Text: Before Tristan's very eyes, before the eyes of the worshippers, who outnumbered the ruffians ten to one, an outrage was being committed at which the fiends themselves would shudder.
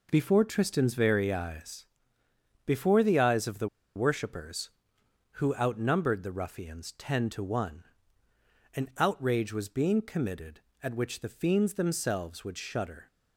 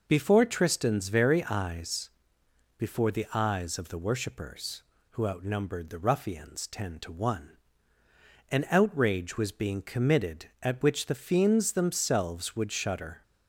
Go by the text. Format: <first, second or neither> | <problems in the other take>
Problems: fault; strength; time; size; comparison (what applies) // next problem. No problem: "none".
second | pauses between "the" and "worshippers"; slight; at 3.6 s; 0.27 s long